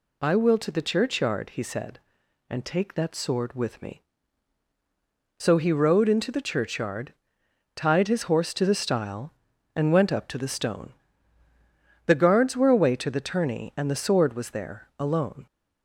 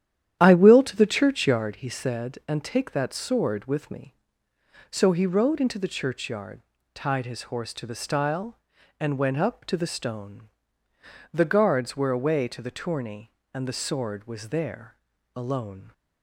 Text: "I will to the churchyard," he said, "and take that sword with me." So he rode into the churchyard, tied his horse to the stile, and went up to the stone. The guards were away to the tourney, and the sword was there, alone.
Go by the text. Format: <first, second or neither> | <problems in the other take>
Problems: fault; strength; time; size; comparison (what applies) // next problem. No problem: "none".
first | starts louder than the rest; strong; until 1.8 s; 10.5 dB